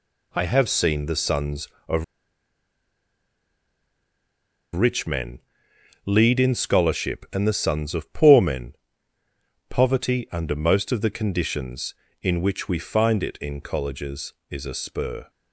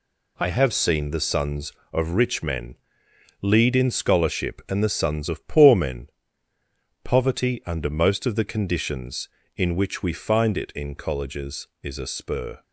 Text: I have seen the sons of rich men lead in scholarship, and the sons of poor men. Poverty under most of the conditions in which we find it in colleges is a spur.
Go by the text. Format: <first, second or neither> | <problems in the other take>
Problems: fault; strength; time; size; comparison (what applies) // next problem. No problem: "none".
second | pauses between "of" and "rich"; strong; at 2.0 s; 2.7 s long // pauses between "men" and "lead"; noticeable; at 5.3 s; 0.64 s long; noticeable in the second